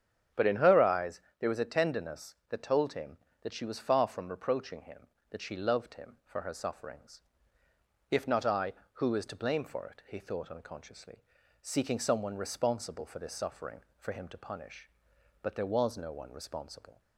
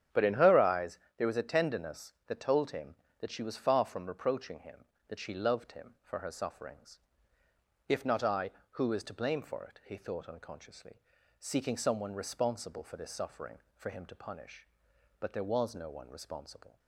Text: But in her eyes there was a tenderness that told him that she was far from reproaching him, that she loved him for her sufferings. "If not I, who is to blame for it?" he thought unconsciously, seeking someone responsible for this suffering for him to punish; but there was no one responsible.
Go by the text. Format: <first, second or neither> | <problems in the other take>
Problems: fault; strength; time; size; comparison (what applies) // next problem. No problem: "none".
first | gets quieter; strong; throughout; 10 dB // starts louder than the rest; strong; until 1.3 s; 9 dB; strong in the first // pauses between "eyes" and "there"; slight; at 0.9 s; 0.18 s long; slight in the first